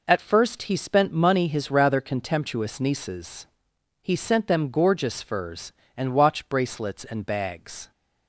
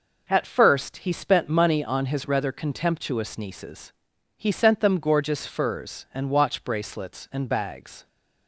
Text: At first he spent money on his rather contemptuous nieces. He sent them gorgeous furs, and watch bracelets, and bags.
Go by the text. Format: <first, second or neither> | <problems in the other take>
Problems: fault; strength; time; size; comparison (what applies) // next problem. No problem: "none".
second | skips "on"; at 1.4 s